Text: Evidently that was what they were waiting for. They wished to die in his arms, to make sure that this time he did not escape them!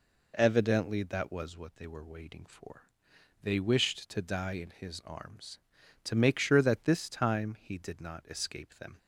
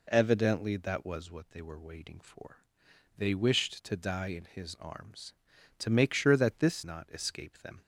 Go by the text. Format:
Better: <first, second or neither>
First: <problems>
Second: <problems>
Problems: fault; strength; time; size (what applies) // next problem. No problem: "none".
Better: first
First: none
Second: skips "time he did"; at 6.8 s